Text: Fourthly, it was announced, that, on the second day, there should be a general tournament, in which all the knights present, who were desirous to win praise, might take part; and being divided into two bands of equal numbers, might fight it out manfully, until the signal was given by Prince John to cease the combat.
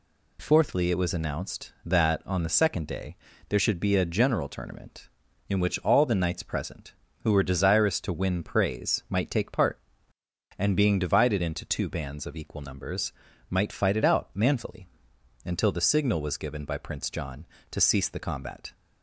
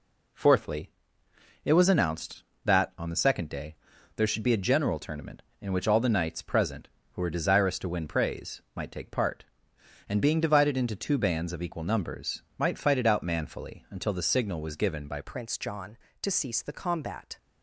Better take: first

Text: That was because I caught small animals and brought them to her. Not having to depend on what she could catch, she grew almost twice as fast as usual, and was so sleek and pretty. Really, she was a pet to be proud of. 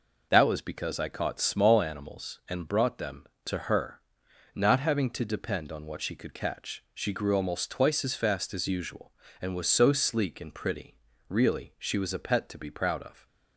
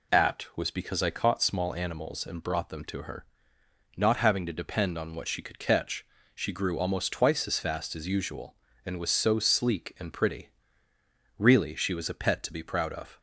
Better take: first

